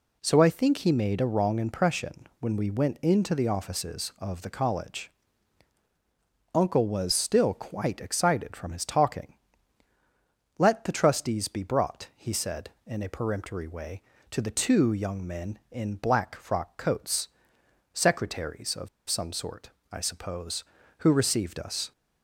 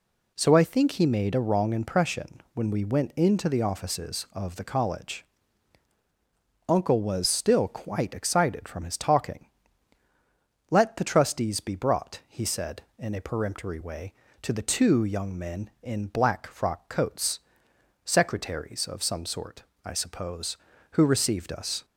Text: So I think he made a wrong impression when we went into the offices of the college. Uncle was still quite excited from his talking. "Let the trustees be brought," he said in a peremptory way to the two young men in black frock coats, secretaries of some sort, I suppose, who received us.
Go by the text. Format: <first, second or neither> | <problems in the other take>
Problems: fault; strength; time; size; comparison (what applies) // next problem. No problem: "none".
second | pauses between "of" and "some"; slight; at 18.8 s; 0.21 s long